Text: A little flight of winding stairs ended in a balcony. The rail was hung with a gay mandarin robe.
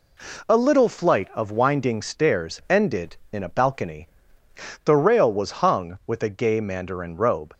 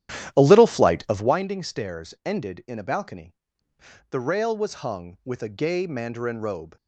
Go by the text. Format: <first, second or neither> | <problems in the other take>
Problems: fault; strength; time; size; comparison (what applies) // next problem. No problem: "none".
first | starts louder than the rest; strong; until 1.4 s; 11.5 dB